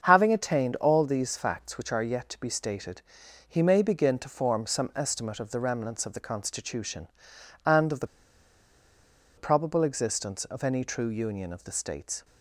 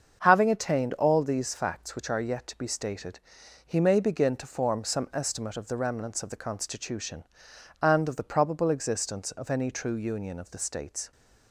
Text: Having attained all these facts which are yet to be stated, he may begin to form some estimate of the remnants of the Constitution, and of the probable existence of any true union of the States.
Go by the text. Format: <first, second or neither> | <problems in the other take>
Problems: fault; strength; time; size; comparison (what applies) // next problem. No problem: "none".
second | starts louder than the rest; until 1.0 s; 7 dB; also in the second // pauses between "the" and "probable"; strong; at 8.0 s; 1.2 s long